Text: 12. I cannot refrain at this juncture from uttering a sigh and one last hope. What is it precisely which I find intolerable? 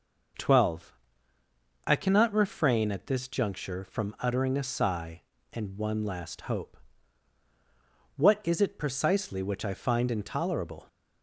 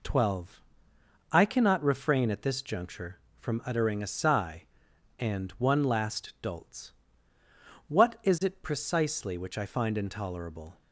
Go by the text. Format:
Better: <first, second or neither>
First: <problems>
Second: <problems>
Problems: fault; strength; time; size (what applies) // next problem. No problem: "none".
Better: first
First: none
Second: says "dolts" for "hope"; at 6.4 s